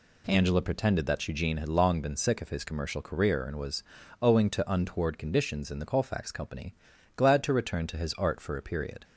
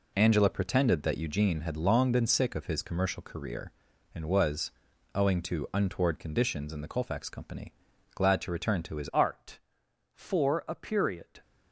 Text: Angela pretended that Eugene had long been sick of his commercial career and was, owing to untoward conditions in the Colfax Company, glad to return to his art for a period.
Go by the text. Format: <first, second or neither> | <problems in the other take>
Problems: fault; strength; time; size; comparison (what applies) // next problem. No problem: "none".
first | changes voice at "art"; from 9.1 s on; 2.3 s long